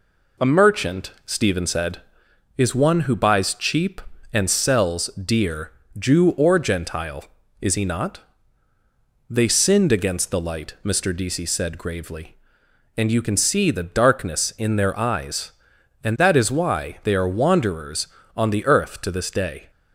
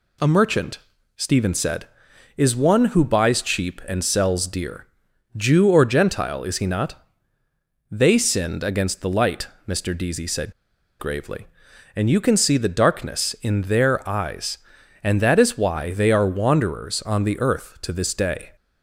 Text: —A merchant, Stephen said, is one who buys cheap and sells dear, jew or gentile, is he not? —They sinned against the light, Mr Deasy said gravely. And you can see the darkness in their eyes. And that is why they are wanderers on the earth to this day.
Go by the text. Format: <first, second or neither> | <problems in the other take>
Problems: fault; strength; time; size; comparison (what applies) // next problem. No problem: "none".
first | pauses between "said" and "gravely"; noticeable; at 10.5 s; 0.48 s long